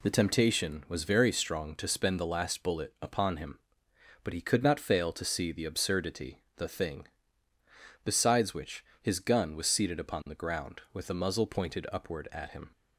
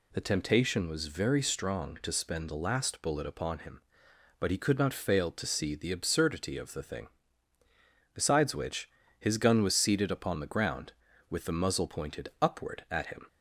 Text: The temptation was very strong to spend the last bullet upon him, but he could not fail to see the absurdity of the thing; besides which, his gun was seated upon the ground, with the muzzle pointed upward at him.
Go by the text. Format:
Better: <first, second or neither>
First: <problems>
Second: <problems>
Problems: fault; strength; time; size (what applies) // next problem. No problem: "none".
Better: second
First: skips "of"; at 6.4 s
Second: none